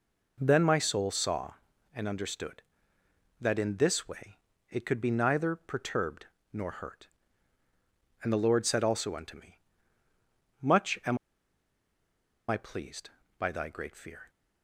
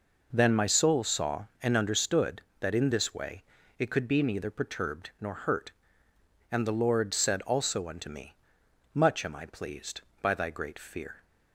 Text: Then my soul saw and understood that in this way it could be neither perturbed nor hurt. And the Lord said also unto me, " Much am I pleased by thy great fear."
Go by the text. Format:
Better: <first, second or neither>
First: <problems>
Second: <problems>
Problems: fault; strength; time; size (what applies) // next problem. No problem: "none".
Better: second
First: pauses between "way" and "it"; slight; at 4.3 s; 0.34 s long // pauses between "perturbed" and "nor"; slight; at 6.2 s; 0.26 s long // pauses between "am" and "I"; strong; at 11.1 s; 1.3 s long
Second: pauses between "way" and "it"; slight; at 3.4 s; 0.36 s long